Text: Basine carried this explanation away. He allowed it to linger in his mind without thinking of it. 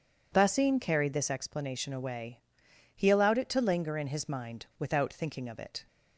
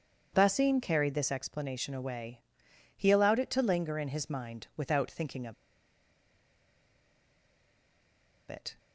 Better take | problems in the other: first | pauses between "of" and "it"; strong; at 5.5 s; 2.9 s long

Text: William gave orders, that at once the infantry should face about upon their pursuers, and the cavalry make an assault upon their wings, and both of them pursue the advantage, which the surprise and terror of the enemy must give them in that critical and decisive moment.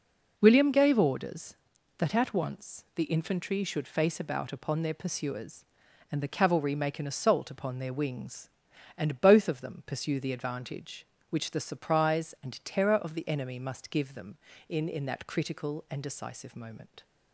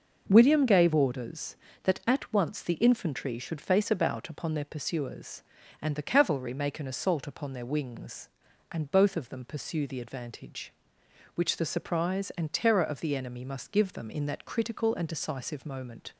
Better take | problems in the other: second | says "in" twice; at 14.8 s

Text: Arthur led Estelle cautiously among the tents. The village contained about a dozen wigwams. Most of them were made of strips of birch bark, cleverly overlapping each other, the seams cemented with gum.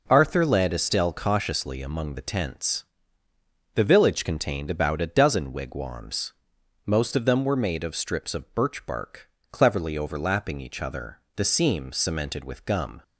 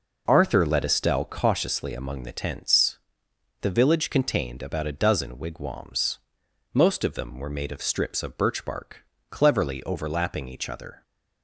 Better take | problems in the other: first | stops before "the seams cemented with gum"; at 11.0 s

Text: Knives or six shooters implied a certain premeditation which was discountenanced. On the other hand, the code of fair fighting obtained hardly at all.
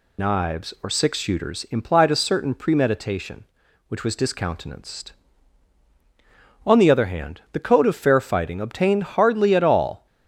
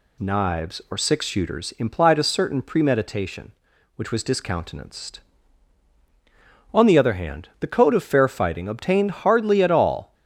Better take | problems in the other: second | loses the start of "Knives"; at 0.1 s; 65 ms

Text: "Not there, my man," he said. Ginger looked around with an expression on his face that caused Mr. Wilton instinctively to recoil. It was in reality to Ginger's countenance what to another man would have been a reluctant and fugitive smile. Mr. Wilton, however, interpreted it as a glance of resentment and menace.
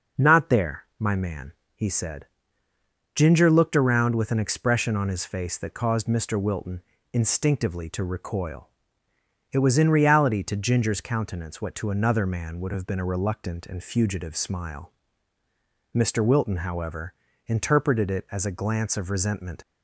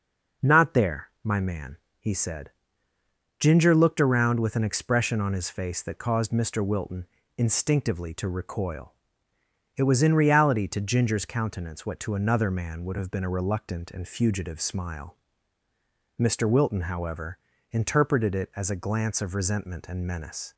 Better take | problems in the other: second | pauses between "Wilton" and "instinctively"; slight; at 6.8 s; 0.30 s long; slight in the second // stops before "and menace"; at 19.6 s

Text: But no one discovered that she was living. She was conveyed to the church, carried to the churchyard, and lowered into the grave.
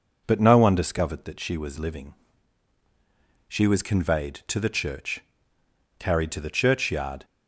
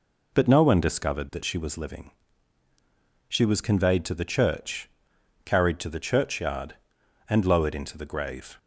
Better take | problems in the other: second | stops before "and lowered into the grave"; at 7.2 s

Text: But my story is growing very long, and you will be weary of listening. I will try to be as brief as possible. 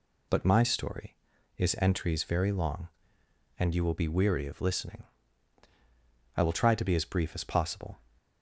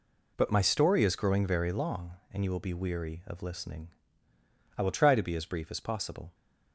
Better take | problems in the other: second | says "entries" for "growing"; at 1.7 s

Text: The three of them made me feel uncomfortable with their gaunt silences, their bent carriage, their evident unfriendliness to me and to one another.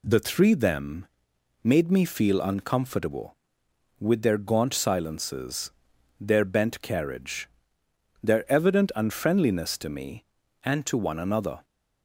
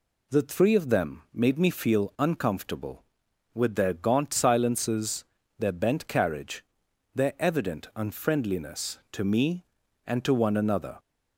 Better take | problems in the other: second | skips "of"; at 0.5 s // pauses between "them" and "made"; noticeable; at 1.0 s; 0.56 s long

